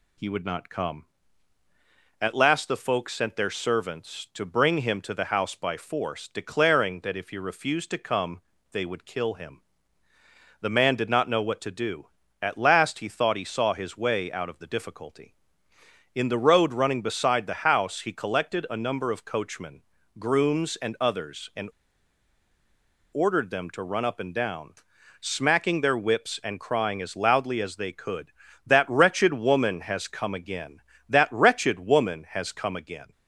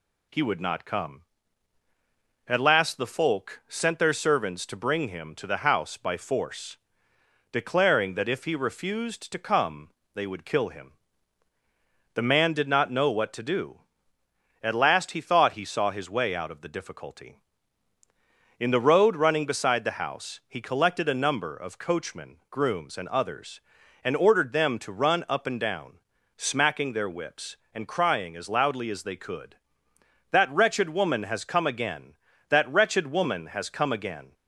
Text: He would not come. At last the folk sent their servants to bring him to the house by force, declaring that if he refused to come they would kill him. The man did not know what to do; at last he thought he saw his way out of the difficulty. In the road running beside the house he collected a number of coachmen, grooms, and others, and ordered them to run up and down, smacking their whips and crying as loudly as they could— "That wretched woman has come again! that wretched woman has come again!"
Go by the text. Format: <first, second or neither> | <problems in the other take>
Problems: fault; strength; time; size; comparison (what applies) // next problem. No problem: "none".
second | pauses between "come" and "they"; slight; at 8.4 s; 0.32 s long; slight in the second // pauses between "and" and "ordered"; strong; at 21.7 s; 1.4 s long